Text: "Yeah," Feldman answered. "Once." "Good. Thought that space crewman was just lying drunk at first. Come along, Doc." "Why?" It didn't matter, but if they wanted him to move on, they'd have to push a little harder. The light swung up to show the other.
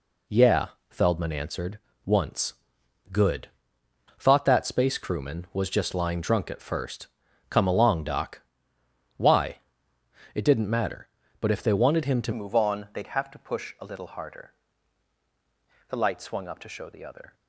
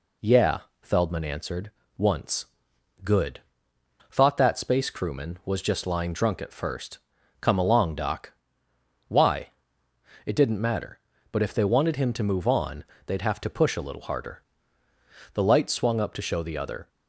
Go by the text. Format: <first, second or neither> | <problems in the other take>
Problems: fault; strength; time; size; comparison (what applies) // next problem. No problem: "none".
second | changes voice at "move"; from 12.3 s on; 5.0 s long